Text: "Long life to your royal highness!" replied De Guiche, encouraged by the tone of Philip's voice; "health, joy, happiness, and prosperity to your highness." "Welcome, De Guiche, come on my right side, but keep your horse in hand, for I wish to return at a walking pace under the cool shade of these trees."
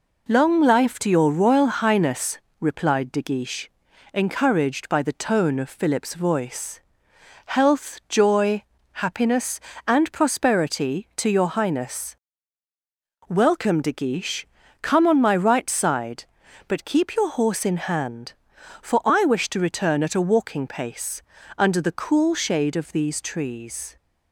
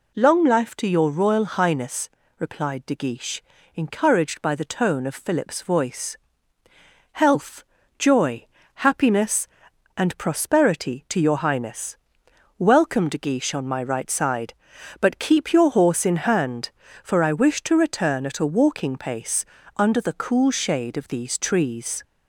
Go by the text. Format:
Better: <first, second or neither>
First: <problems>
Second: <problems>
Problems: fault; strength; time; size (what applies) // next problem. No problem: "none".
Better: first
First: pauses between "pace" and "under"; slight; at 21.2 s; 0.34 s long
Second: skips "come"; at 13.5 s // pauses between "pace" and "under"; slight; at 19.4 s; 0.32 s long